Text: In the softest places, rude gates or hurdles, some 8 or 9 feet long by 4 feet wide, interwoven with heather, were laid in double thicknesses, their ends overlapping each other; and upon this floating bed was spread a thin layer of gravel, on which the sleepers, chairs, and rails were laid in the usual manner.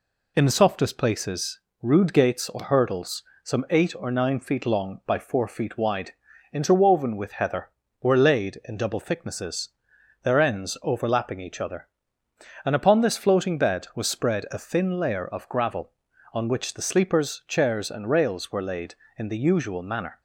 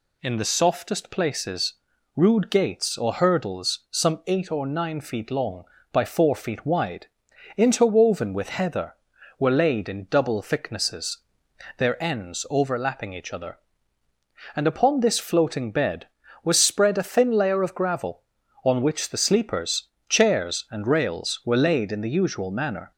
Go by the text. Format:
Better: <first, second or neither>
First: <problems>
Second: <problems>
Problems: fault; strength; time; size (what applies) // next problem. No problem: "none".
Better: neither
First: none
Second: none